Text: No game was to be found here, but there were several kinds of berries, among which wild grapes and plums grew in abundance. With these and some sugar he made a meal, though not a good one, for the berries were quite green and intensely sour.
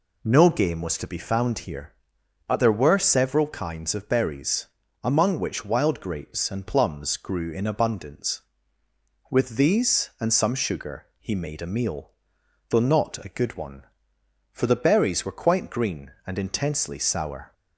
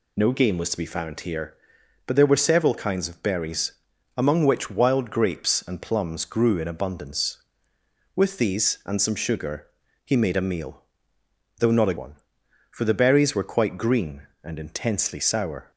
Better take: first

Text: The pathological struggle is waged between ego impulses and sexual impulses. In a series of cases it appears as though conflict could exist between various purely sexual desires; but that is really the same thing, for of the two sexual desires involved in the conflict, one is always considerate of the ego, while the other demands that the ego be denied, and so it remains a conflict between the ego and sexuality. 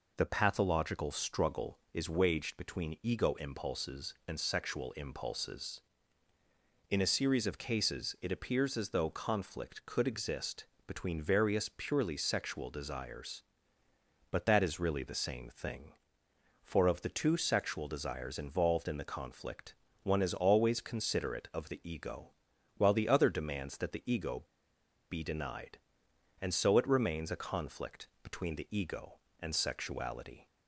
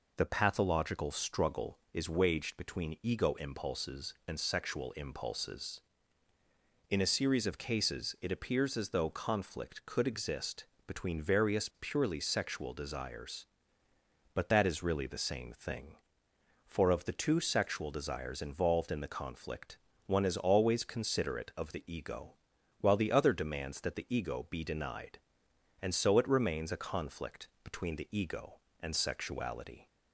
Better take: second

